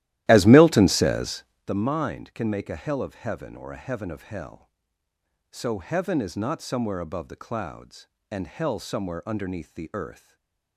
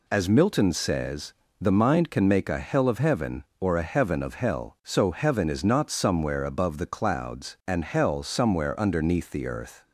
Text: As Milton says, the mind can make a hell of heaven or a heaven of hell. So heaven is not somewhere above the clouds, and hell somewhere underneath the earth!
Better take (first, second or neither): second